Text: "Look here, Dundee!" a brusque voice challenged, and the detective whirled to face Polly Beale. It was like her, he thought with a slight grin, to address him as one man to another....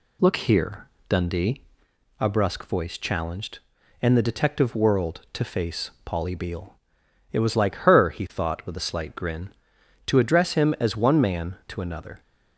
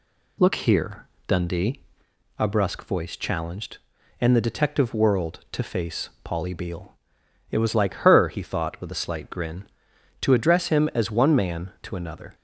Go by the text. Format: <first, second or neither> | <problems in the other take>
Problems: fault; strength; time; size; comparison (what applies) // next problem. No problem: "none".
neither | none